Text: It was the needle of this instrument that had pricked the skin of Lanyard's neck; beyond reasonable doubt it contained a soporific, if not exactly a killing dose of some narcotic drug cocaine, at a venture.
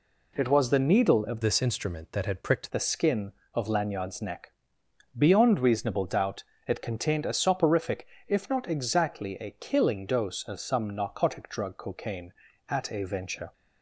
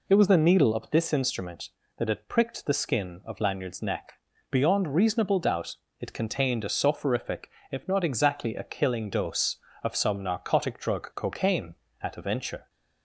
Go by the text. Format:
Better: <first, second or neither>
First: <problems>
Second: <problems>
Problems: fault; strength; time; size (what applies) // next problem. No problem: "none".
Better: second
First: changes voice from "this" to "pricked"; from 1.4 to 2.7 s; 1.3 s long // pauses between "doubt" and "it"; slight; at 6.4 s; 0.24 s long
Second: pauses between "doubt" and "it"; slight; at 5.7 s; 0.24 s long